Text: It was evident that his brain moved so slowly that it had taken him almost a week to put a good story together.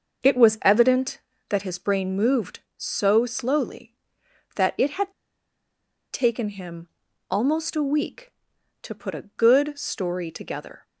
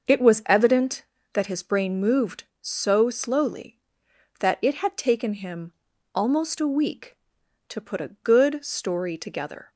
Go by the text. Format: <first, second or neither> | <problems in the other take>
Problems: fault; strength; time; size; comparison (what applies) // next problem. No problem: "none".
second | starts louder than the rest; until 1.5 s; 6 dB; also in the second // pauses between "had" and "taken"; at 5.1 s; 1.0 s long // pauses between "him" and "almost"; at 6.8 s; 0.42 s long; also in the second